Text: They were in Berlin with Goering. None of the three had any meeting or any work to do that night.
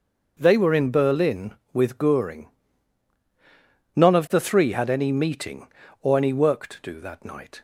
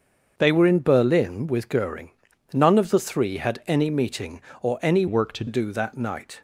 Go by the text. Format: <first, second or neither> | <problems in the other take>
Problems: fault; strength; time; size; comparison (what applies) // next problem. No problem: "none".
first | starts louder than the rest; until 1.3 s; 6.5 dB // changes voice from "work" to "to"; from 5.0 to 5.4 s; 0.4 s long